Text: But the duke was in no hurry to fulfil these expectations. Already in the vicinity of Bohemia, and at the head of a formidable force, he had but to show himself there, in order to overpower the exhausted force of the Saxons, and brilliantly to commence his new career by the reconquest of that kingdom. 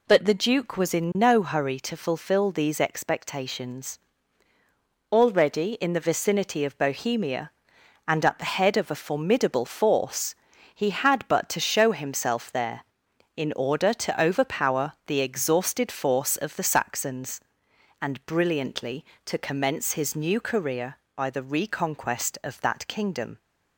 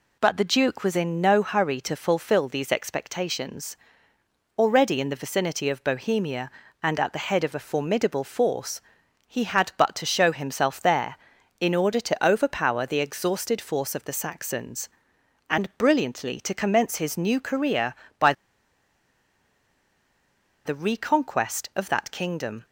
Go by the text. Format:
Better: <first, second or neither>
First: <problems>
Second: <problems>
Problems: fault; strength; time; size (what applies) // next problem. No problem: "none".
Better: first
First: none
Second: pauses between "by" and "the"; strong; at 18.3 s; 2.3 s long